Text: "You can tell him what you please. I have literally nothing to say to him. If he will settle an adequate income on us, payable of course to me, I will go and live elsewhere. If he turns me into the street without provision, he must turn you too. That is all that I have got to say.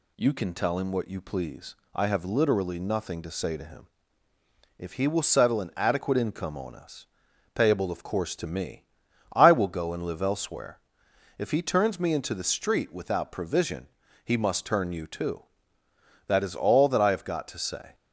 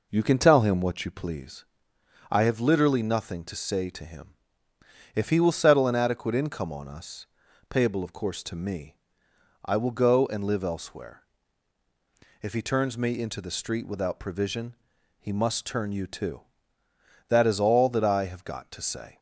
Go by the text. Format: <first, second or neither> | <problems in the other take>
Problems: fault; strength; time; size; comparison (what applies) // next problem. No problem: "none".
neither | none